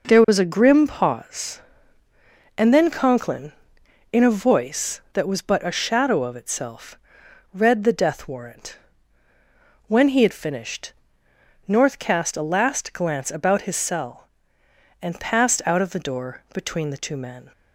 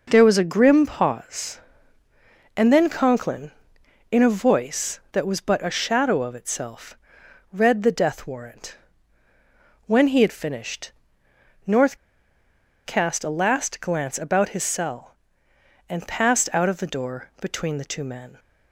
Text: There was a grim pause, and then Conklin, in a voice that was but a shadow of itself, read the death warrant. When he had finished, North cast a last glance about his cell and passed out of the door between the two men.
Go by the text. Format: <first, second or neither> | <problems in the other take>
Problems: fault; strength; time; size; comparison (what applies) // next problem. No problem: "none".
first | pauses between "North" and "cast"; noticeable; at 11.9 s; 0.89 s long